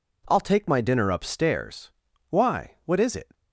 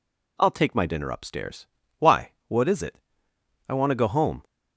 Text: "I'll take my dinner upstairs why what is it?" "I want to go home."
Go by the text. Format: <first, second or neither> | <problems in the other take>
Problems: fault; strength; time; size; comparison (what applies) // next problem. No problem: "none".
second | pauses between "upstairs" and "why"; at 1.9 s; 0.42 s long; slight in the second // stops before "I want to go home"; at 3.3 s